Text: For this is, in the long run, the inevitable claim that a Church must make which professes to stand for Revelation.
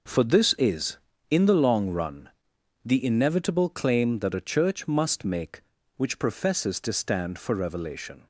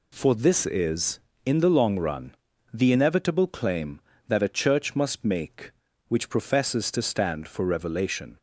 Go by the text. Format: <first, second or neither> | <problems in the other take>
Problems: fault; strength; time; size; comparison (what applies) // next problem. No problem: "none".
neither | none